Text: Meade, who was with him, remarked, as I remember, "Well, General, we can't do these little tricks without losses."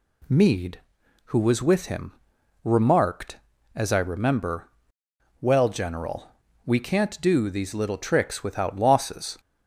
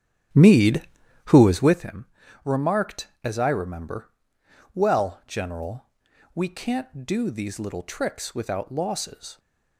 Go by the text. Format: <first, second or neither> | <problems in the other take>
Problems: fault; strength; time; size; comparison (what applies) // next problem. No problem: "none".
first | starts louder than the rest; strong; until 1.9 s; 10.5 dB